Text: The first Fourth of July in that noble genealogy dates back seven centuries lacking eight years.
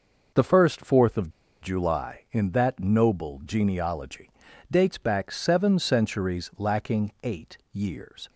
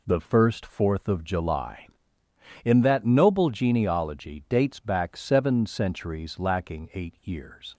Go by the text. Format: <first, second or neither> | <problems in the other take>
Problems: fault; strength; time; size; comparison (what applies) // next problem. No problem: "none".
second | pauses between "of" and "July"; slight; at 1.2 s; 0.33 s long // pauses between "genealogy" and "dates"; at 4.3 s; 0.40 s long // pauses between "eight" and "years"; slight; at 7.5 s; 0.16 s long